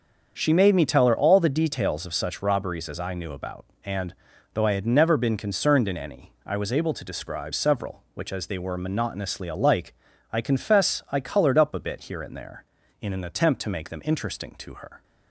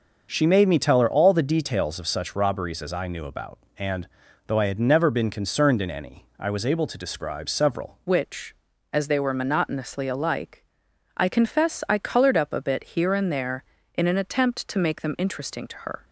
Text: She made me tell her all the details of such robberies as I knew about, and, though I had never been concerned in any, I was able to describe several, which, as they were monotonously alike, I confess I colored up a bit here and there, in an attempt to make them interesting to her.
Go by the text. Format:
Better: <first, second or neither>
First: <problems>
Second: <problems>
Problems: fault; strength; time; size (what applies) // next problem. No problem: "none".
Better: first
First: starts louder than the rest; until 1.3 s; 7 dB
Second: starts louder than the rest; until 1.3 s; 6.5 dB // changes voice at "which"; from 8.0 s on; 8.0 s long